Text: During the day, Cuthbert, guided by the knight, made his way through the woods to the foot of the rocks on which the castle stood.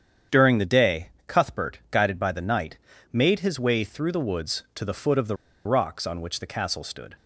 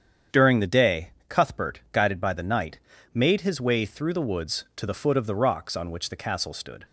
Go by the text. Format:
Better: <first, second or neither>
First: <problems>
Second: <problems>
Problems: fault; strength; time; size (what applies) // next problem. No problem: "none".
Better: second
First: starts louder than the rest; strong; until 1.4 s; 8.5 dB // pauses between "the" and "rocks"; slight; at 5.3 s; 0.29 s long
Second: starts louder than the rest; strong; until 1.5 s; 8 dB